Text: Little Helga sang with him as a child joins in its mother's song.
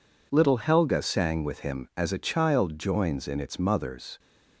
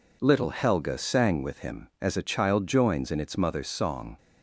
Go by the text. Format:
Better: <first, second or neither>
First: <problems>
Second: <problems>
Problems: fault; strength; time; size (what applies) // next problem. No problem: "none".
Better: second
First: stops before "song"; at 4.1 s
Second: none